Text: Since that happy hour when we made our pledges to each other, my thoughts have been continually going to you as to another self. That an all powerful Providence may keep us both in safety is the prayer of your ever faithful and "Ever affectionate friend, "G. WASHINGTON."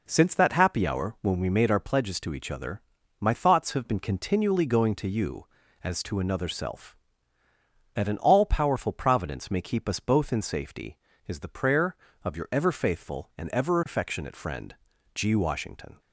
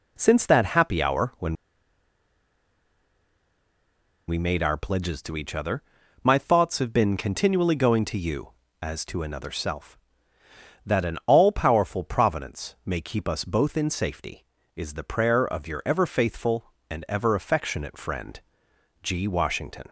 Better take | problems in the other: first | pauses between "when" and "we"; strong; at 1.5 s; 2.7 s long

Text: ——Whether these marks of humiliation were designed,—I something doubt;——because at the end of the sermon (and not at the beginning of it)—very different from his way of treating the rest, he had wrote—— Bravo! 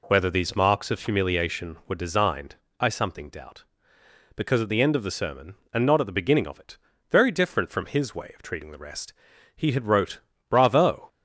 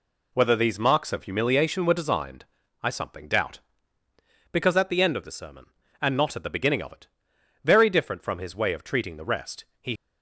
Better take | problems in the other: first | stops before "had wrote Bravo"; at 9.9 s

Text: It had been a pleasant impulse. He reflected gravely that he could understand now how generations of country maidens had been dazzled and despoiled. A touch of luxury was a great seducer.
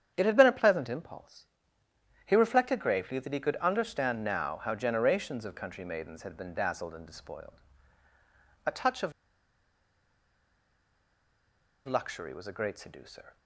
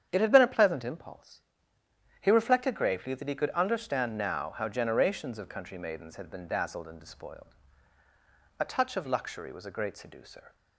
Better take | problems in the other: second | starts louder than the rest; strong; until 1.1 s; 8.5 dB; strong in the second // pauses between "of" and "luxury"; strong; at 9.1 s; 2.7 s long

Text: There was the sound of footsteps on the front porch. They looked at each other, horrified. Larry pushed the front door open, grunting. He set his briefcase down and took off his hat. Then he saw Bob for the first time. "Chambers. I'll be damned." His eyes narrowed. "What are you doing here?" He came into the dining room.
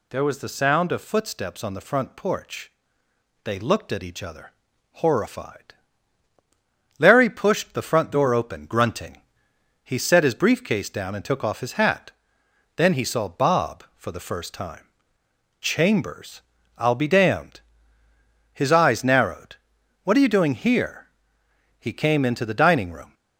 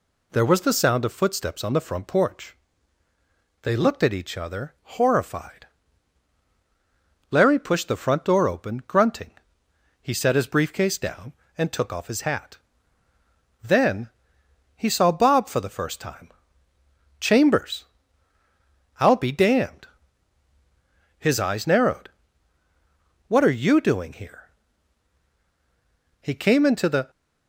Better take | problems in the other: first | pauses between "Then" and "he"; noticeable; at 14.0 s; 0.66 s long // stops before "dining room"; at 27.0 s

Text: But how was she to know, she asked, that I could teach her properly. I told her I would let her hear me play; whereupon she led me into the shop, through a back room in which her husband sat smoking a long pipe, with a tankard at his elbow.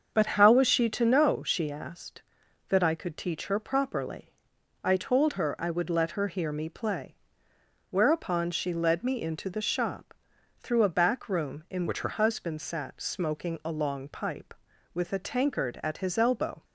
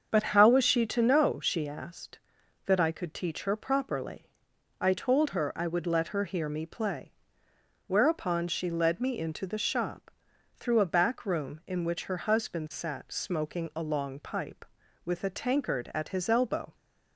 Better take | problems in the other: second | starts louder than the rest; until 1.1 s; 6.5 dB; also in the second // changes voice from "which" to "her"; from 11.8 to 12.0 s; 0.2 s long

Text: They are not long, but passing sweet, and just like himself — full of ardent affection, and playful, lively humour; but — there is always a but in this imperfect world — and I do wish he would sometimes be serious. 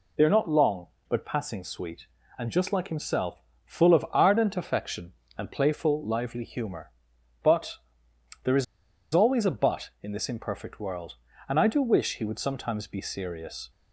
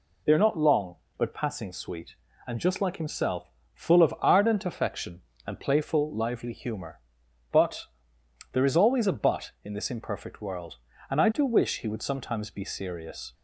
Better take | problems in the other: second | pauses between "is" and "always"; noticeable; at 8.6 s; 0.49 s long

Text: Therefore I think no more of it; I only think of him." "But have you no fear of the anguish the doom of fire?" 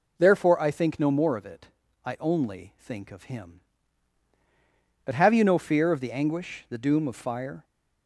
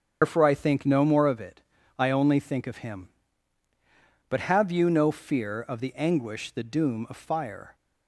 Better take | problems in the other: first | loses the start of "Therefore"; at 0.2 s; 130 ms // starts louder than the rest; strong; until 1.2 s; 7 dB

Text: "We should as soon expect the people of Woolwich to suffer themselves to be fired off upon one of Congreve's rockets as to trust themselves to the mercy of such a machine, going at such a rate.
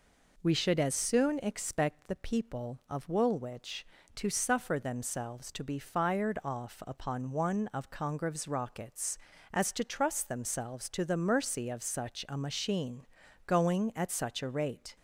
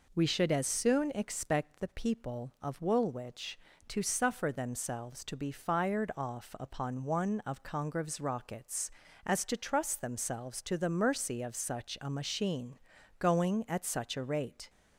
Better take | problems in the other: neither | none

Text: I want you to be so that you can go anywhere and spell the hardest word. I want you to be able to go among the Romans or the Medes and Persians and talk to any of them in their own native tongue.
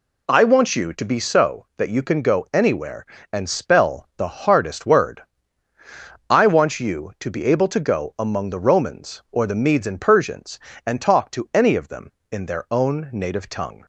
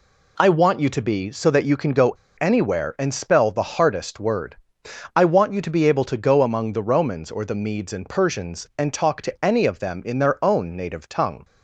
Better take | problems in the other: first | pauses between "go" and "anywhere"; slight; at 2.1 s; 0.26 s long

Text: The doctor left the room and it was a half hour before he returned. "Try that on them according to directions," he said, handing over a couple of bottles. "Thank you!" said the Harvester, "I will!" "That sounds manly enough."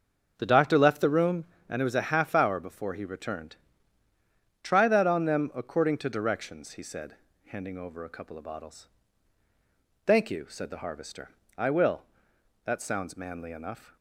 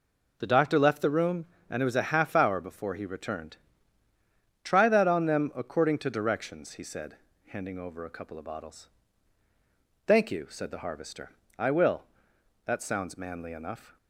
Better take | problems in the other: second | starts louder than the rest; until 1.7 s; 6.5 dB

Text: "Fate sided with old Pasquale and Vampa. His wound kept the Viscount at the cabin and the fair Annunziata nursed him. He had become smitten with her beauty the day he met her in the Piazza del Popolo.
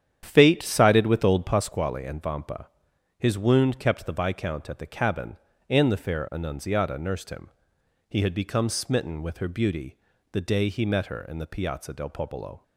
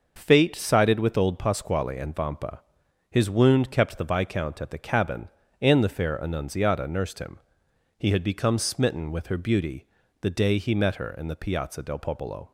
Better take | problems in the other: second | starts louder than the rest; strong; until 1.8 s; 9.5 dB // pauses between "beauty" and "the"; slight; at 9.9 s; 0.36 s long; slight in the second

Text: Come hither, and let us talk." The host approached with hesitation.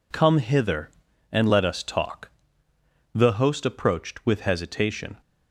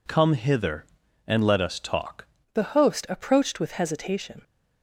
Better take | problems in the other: first | changes voice at "The"; from 2.5 s on; 1.9 s long

